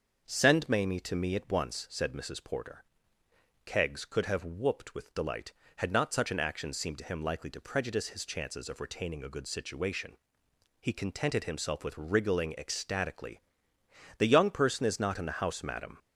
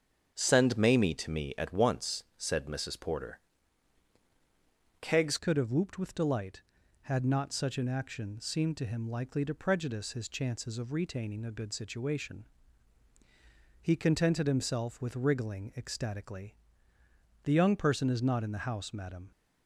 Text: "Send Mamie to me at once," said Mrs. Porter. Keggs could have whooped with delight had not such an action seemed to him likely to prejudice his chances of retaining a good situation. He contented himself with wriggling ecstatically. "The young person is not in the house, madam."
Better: first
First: starts louder than the rest; until 1.2 s; 6.5 dB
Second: starts louder than the rest; until 1.3 s; 7 dB // changes voice at "could"; from 5.3 s on; 14.0 s long

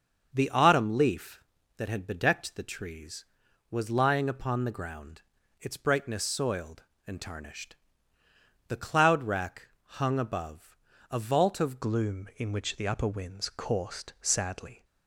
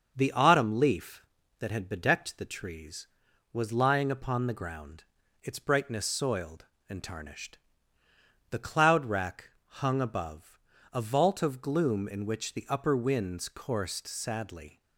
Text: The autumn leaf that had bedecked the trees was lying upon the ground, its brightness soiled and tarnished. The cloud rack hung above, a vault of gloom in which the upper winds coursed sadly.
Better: second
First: starts louder than the rest; until 1.3 s; 6.5 dB // pauses between "rack" and "hung"; slight; at 9.6 s; 0.16 s long // changes voice at "gloom"; from 11.8 s on; 3.0 s long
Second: starts louder than the rest; until 1.1 s; 6.5 dB // pauses between "rack" and "hung"; slight; at 9.4 s; 0.16 s long

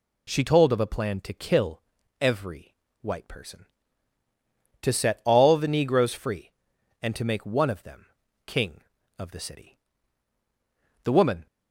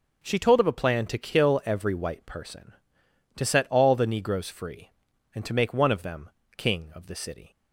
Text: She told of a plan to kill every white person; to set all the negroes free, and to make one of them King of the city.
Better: second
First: pauses between "kill" and "every"; at 1.8 s; 0.40 s long // pauses between "every" and "white"; slight; at 2.7 s; 0.26 s long // pauses between "them" and "King"; at 8.0 s; 0.40 s long // goes on to say "The woman"; slight; from 11.0 s on; 0.42 s long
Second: pauses between "them" and "King"; slight; at 6.3 s; 0.26 s long

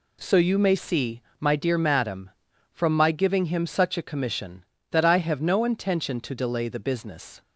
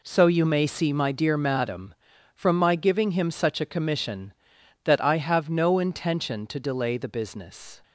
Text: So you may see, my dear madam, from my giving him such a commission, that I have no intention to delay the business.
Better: neither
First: none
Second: none

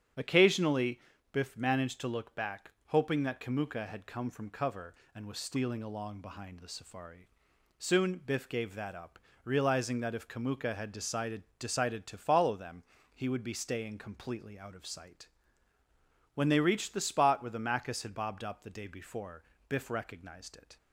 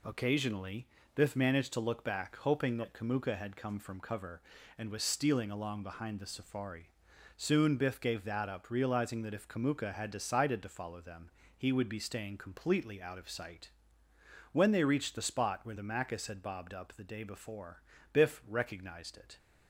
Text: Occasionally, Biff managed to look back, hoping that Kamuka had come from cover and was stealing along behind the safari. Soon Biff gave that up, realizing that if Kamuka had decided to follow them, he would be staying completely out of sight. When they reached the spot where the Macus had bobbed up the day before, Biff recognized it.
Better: second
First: starts louder than the rest; strong; until 1.4 s; 9.5 dB // says "decided" twice; at 11.5 s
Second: none

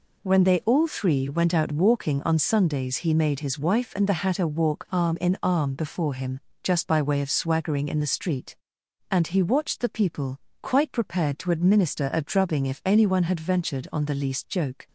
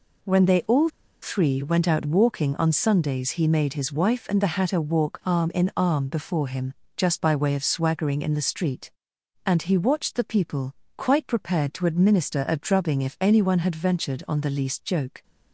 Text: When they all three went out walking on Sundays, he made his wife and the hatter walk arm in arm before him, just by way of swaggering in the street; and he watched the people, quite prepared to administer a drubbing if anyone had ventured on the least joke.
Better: first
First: none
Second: pauses between "all" and "three"; slight; at 0.9 s; 0.32 s long

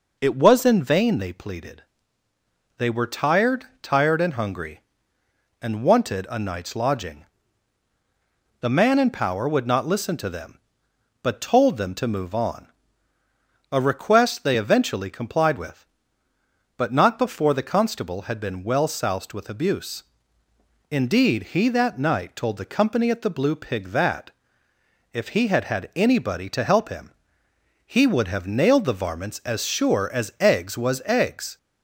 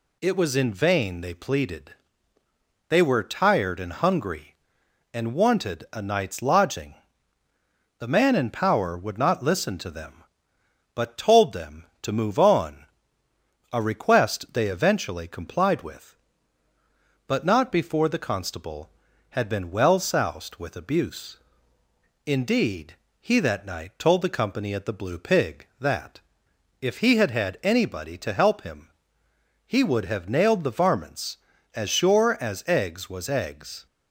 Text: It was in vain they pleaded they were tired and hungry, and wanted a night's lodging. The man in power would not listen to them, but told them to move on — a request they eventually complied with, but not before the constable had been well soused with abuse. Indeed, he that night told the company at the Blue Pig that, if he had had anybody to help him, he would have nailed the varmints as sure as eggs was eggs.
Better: second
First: pauses between "pleaded" and "they"; noticeable; at 1.8 s; 0.94 s long // says "tired" twice; at 3.8 s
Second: pauses between "pleaded" and "they"; noticeable; at 1.9 s; 0.96 s long

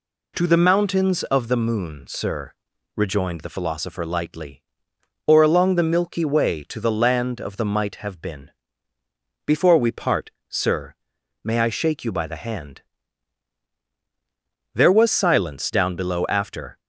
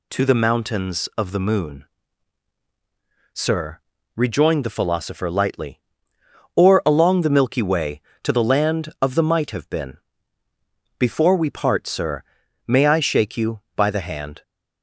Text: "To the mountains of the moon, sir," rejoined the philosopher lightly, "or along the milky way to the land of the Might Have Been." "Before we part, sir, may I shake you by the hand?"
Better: second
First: goes on to say "There was silence down below after"; strong; from 14.7 s on; 2.0 s long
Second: none

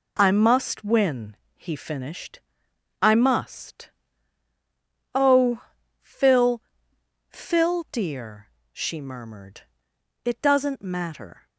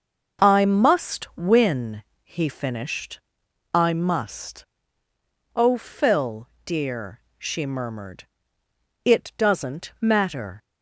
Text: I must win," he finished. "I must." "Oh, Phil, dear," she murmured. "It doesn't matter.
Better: second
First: says "Phil" twice; at 7.2 s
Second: none

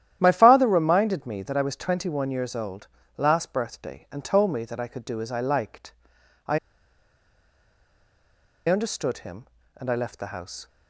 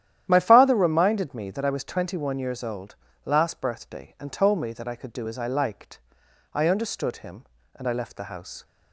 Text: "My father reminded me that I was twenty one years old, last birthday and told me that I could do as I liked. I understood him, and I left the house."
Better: second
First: starts louder than the rest; strong; until 1.2 s; 11.5 dB // pauses between "I" and "understood"; strong; at 6.5 s; 2.1 s long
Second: starts louder than the rest; strong; until 1.3 s; 11 dB

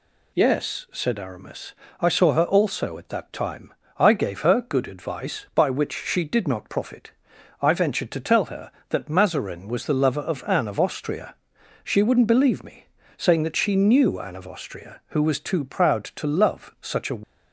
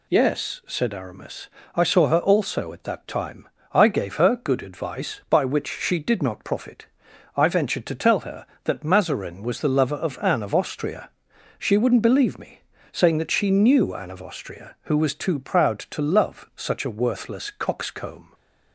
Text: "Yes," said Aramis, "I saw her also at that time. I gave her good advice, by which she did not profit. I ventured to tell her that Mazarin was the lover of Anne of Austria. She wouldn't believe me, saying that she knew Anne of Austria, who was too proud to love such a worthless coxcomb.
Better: second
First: stops before "worthless coxcomb"; at 17.2 s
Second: none

